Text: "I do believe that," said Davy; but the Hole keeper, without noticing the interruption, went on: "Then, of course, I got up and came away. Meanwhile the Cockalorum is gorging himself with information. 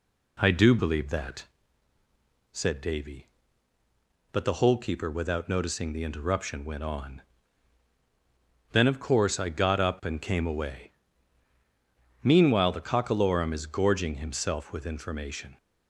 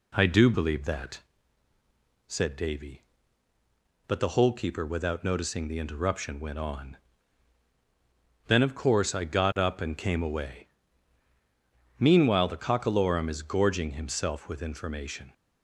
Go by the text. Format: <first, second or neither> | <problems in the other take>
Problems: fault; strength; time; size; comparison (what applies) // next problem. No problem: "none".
neither | none